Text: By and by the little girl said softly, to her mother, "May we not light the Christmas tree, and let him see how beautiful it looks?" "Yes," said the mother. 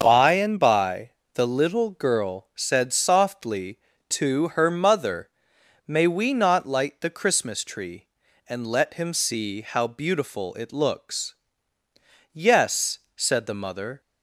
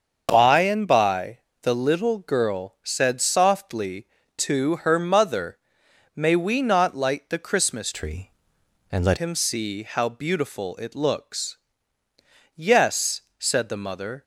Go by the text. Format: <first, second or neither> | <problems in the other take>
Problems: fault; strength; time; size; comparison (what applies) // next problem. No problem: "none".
first | starts louder than the rest; until 1.3 s; 6.5 dB; also in the first // pauses between "by" and "the"; slight; at 1.3 s; 0.22 s long; slight in the first // changes voice from "tree" to "let"; from 7.9 to 9.1 s; 1.2 s long